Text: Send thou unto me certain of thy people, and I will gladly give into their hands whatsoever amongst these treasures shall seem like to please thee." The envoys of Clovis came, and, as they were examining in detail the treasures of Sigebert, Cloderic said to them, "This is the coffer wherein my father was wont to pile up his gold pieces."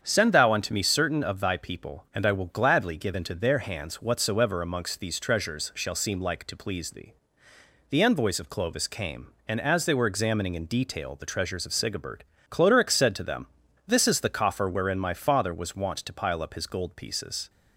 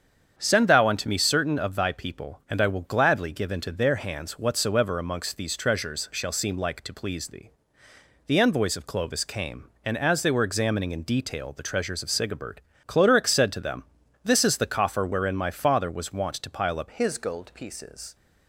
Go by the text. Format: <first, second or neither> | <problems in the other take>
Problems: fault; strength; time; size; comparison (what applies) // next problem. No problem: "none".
first | starts louder than the rest; strong; until 1.3 s; 8 dB; strong in the first // changes voice at "his"; from 16.9 s on; 1.2 s long